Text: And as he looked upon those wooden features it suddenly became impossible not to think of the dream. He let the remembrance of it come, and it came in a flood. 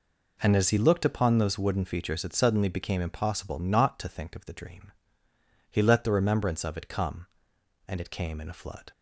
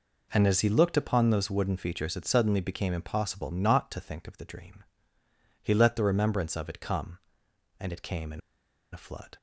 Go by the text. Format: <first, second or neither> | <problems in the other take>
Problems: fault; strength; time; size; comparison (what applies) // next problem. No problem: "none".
first | pauses between "in" and "a"; noticeable; at 8.4 s; 0.52 s long